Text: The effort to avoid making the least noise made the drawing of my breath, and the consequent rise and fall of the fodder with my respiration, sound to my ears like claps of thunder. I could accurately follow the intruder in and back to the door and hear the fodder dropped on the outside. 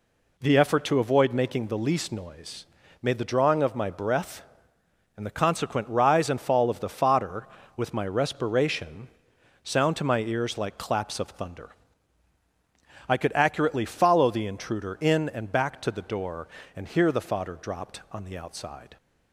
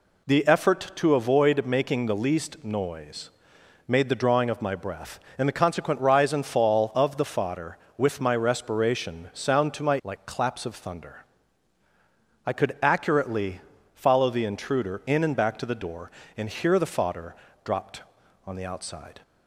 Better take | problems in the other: first | pauses between "noise" and "made"; noticeable; at 3.2 s; 0.58 s long; slight in the first // skips "ears"; at 10.0 s // pauses between "accurately" and "follow"; slight; at 13.5 s; 0.34 s long // pauses between "fodder" and "dropped"; slight; at 17.3 s; 0.30 s long

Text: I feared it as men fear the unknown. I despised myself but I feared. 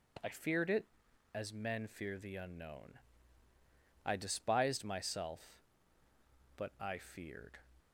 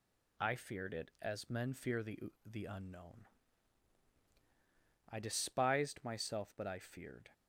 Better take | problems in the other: first | says "the" twice; at 2.4 s

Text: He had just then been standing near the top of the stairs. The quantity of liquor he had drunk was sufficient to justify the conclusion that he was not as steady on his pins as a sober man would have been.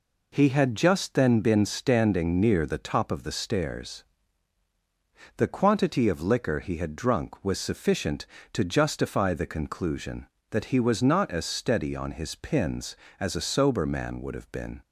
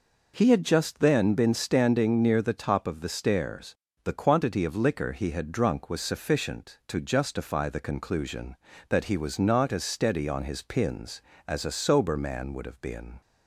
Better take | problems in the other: neither | none

